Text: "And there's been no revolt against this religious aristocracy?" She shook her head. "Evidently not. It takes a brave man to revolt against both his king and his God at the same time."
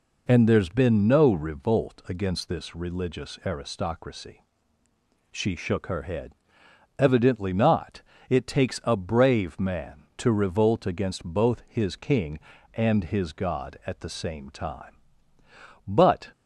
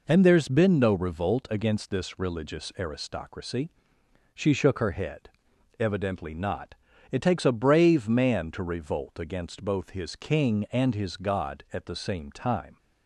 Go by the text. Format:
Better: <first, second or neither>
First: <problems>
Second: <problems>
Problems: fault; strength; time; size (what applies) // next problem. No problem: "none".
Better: second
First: goes on to say "But"; slight; from 15.8 s on; 0.44 s long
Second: none